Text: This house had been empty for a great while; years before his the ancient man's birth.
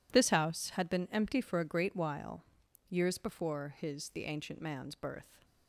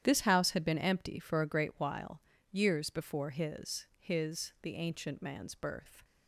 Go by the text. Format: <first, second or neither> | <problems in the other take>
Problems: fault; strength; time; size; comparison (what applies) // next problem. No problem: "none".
first | starts louder than the rest; strong; until 1.0 s; 10 dB // says "his" twice; at 4.0 s